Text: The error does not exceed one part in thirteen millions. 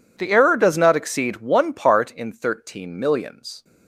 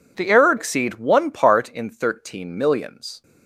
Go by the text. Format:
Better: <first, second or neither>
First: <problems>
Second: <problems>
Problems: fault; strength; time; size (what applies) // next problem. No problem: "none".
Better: first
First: none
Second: skips "does not"; at 0.5 s